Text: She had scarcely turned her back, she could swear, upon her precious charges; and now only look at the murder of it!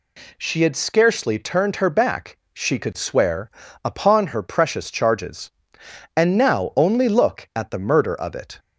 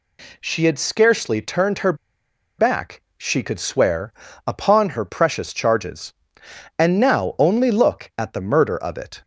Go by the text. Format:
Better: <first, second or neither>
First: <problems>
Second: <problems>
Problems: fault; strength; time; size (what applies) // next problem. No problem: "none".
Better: first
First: none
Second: pauses between "her" and "back"; noticeable; at 1.9 s; 0.64 s long